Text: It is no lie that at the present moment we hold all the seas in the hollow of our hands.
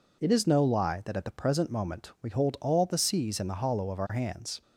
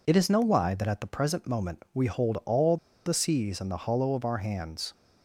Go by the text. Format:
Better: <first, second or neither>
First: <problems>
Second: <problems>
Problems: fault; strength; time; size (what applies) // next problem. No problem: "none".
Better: first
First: none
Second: pauses between "all" and "the"; slight; at 2.7 s; 0.28 s long